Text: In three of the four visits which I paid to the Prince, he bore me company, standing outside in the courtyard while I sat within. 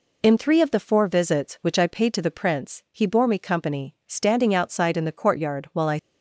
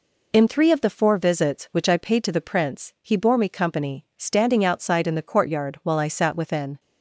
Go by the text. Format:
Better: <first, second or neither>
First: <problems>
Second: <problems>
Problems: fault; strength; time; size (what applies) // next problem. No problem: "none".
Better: second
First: stops before "sat within"; at 5.9 s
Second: none